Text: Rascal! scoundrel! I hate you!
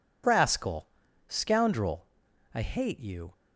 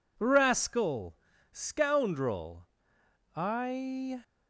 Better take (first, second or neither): first